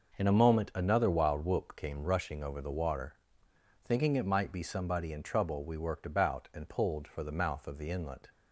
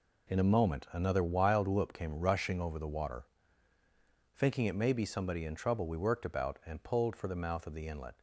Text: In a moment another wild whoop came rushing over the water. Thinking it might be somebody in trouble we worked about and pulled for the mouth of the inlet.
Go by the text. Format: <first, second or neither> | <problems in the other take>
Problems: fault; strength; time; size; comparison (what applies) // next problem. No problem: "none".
first | says "may" for "might"; at 4.7 s